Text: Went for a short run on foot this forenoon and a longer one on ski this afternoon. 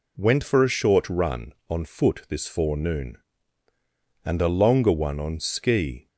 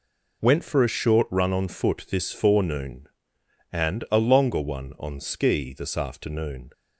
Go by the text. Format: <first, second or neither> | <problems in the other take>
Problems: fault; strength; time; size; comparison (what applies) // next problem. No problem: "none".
second | stops before "this afternoon"; at 6.0 s